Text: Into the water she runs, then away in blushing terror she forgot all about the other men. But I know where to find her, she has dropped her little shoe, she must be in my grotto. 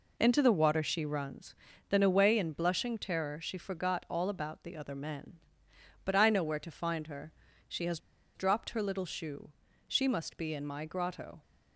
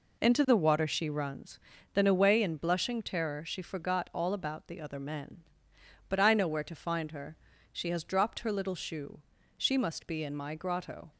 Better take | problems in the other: second | pauses between "has" and "dropped"; at 7.9 s; 0.36 s long

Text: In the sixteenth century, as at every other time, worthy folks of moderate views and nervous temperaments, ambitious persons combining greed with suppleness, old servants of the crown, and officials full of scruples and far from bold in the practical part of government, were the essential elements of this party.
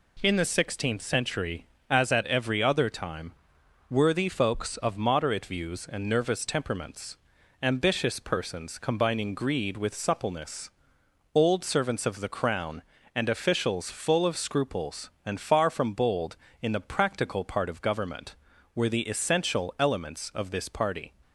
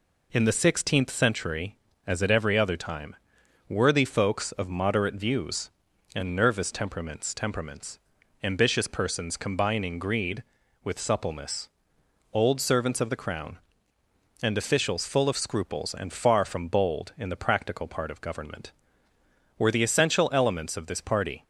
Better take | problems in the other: first | says "temperaments" twice; at 7.3 s

